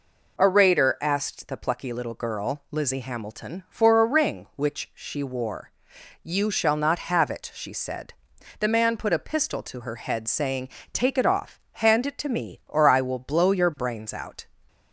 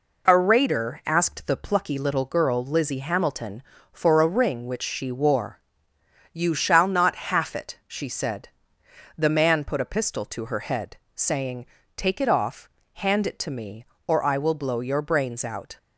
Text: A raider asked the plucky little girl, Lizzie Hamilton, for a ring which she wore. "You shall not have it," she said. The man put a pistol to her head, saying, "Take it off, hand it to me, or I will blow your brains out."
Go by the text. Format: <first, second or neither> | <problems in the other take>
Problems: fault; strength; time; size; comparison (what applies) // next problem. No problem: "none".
first | says "half" for "have"; at 7.3 s